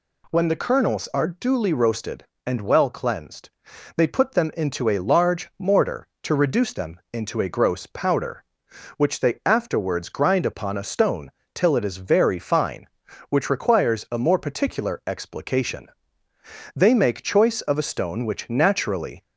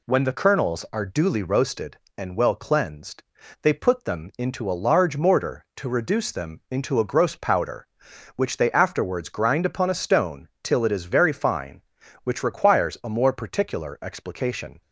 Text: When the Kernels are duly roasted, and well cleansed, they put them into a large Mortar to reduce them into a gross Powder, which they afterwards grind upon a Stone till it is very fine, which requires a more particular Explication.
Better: second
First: pauses between "Stone" and "till"; slight; at 11.2 s; 0.24 s long // goes on to say "They make choice of a Stone which naturally"; strong; from 16.7 s on; 2.4 s long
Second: none

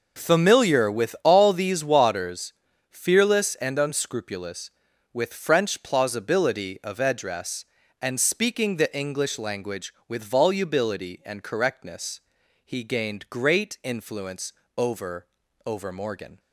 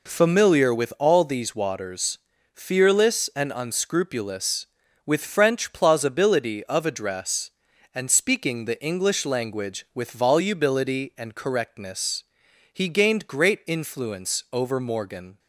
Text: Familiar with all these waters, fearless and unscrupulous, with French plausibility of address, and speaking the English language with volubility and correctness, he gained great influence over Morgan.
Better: second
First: pauses between "influence" and "over"; slight; at 14.5 s; 0.22 s long // says "over" twice; at 15.6 s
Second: none

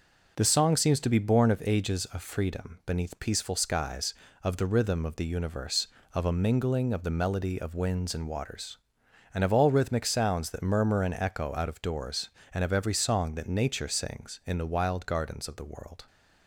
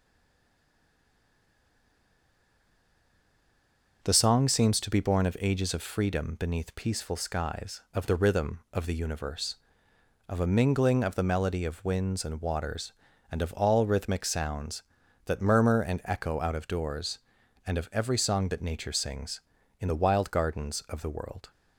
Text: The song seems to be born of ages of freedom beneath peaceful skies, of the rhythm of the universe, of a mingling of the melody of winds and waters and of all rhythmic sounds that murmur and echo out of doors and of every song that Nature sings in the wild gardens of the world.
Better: first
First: none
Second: stays silent before the first word; strong; until 4.0 s; 4.0 s long // starts louder than the rest; noticeable; until 5.0 s; 6 dB

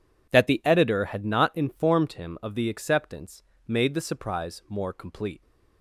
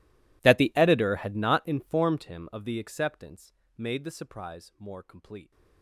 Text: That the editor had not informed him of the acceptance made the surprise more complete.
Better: first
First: pauses between "acceptance" and "made"; slight; at 3.4 s; 0.24 s long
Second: gets quieter; strong; throughout; 25.5 dB // pauses between "acceptance" and "made"; slight; at 3.5 s; 0.24 s long

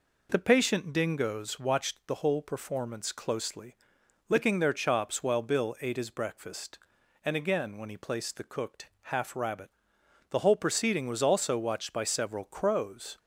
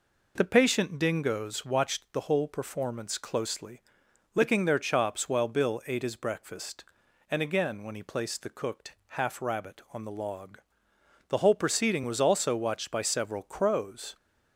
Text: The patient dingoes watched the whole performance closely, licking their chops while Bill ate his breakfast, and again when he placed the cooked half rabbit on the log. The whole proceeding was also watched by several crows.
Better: second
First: pauses between "cooked" and "half"; slight; at 8.8 s; 0.20 s long // skips "on the log"; at 10.0 s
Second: pauses between "cooked" and "half"; slight; at 8.9 s; 0.20 s long

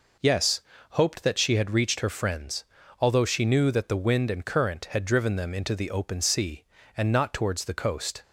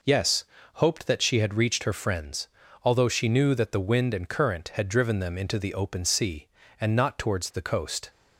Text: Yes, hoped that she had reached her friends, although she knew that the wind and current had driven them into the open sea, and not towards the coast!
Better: neither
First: none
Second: none

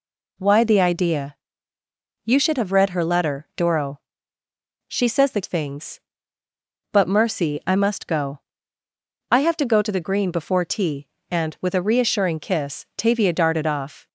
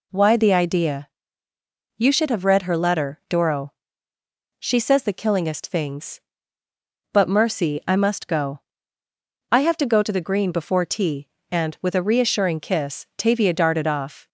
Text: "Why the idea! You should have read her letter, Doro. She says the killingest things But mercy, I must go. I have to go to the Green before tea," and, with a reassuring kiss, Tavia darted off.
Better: second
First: skips "killingest"; at 5.4 s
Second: none

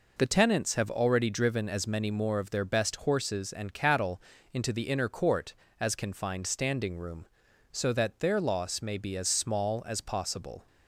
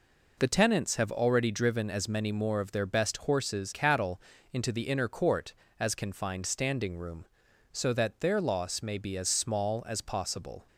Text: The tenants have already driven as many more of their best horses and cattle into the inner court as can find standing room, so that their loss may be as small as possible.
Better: first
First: pauses between "cattle" and "into"; slight; at 4.1 s; 0.32 s long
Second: skips "and"; at 3.7 s // pauses between "cattle" and "into"; slight; at 4.1 s; 0.32 s long

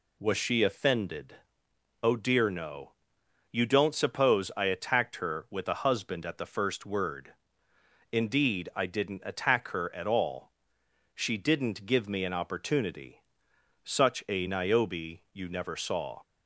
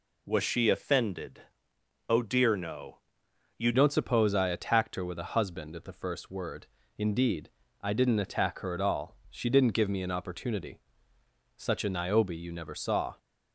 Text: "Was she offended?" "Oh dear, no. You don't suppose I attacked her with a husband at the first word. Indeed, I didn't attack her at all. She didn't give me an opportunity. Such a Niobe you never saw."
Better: first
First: none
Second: changes voice at "don't"; from 3.7 s on; 9.4 s long

